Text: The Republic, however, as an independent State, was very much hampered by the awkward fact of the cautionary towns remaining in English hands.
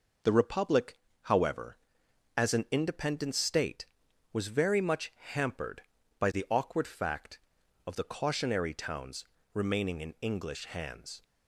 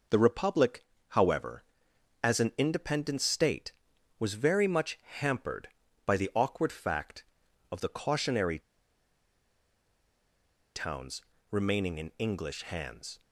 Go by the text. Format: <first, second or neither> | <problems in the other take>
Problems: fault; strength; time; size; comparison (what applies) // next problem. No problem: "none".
first | pauses between "cautionary" and "towns"; strong; at 8.5 s; 2.1 s long // pauses between "towns" and "remaining"; slight; at 11.2 s; 0.28 s long; slight in the first